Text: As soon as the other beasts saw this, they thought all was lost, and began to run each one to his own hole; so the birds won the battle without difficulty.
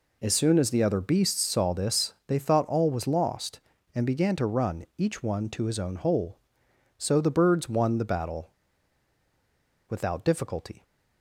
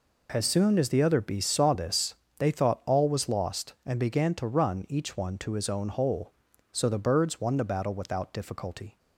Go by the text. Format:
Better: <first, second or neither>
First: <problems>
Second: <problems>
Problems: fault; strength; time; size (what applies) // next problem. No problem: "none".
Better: second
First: pauses between "battle" and "without"; strong; at 8.5 s; 1.3 s long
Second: none